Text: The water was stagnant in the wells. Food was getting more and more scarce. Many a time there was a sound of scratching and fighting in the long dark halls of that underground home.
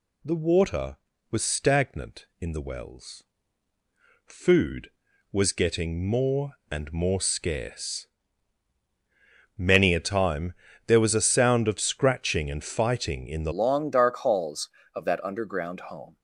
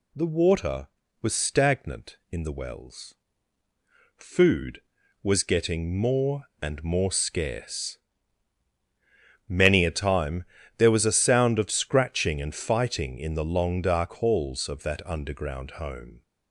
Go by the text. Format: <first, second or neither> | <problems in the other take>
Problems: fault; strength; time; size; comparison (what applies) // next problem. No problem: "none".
second | pauses between "time" and "there"; slight; at 10.5 s; 0.32 s long; slight in the second // changes voice at "long"; from 13.5 s on; 2.6 s long